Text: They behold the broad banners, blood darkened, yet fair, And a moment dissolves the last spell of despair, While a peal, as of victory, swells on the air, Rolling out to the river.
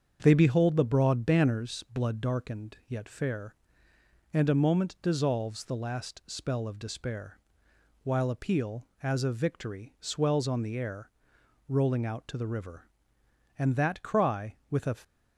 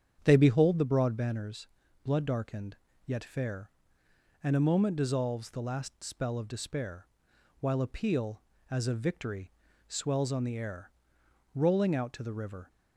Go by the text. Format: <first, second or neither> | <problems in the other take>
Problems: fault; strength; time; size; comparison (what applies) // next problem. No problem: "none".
second | starts louder than the rest; strong; until 1.2 s; 7 dB; strong in the second // goes on to say "And that cry with a"; from 13.5 s on; 1.3 s long